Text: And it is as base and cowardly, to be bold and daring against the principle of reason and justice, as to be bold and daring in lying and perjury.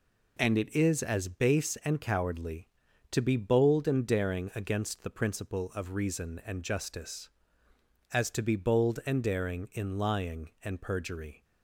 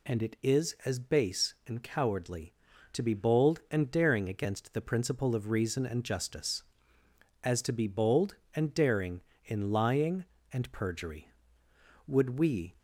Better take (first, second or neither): first